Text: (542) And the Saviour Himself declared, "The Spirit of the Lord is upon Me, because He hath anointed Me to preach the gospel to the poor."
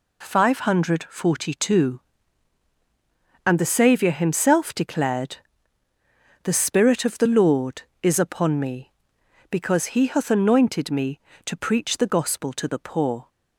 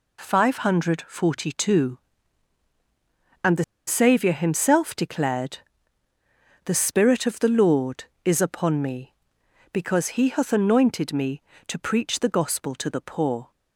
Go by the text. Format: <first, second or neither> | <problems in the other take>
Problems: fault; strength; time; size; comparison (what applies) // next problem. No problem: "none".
first | pauses between "the" and "Saviour"; slight; at 3.6 s; 0.23 s long